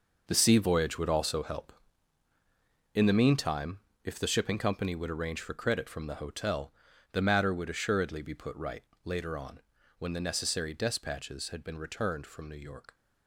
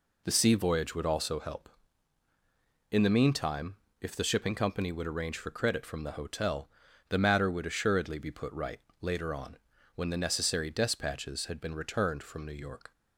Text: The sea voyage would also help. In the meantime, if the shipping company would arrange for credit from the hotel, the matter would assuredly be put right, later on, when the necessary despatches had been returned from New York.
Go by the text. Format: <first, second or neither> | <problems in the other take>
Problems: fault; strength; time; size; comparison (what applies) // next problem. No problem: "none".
second | gets quieter; strong; throughout; 11.5 dB